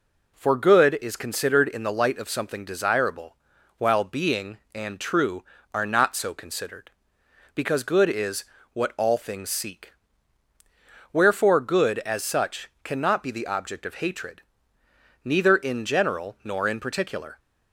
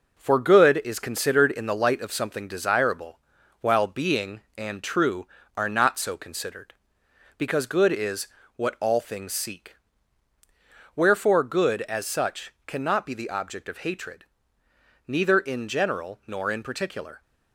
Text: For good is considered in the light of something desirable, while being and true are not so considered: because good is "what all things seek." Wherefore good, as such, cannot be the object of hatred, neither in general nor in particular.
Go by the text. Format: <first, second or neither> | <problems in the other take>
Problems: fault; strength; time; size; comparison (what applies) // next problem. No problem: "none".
first | gets quieter; noticeable; throughout; 5 dB // pauses between "is" and "what"; slight; at 8.2 s; 0.30 s long; slight in the first